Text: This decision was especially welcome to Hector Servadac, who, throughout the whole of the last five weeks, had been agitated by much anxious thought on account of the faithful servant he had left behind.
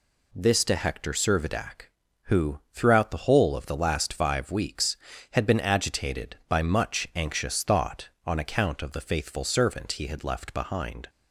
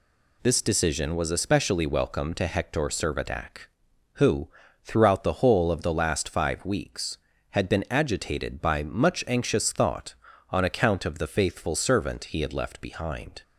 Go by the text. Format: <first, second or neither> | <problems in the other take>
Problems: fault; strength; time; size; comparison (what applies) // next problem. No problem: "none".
second | skips "decision was especially welcome"; at 0.6 s